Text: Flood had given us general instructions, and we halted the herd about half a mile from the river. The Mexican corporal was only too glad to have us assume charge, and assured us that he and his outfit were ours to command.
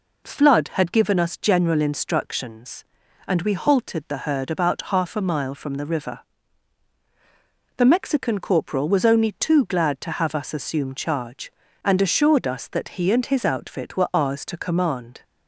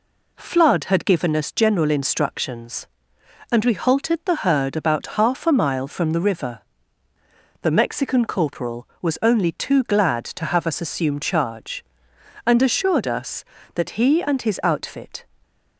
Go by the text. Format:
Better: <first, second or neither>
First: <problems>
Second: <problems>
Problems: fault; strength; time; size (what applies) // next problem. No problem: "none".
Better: first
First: none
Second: stops before "were ours to command"; at 15.4 s